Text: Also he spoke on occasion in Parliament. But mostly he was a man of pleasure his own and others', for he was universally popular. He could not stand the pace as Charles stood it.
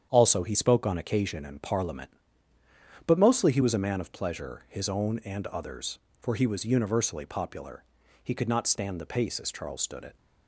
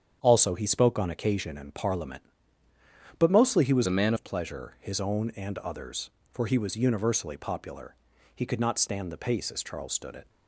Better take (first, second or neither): first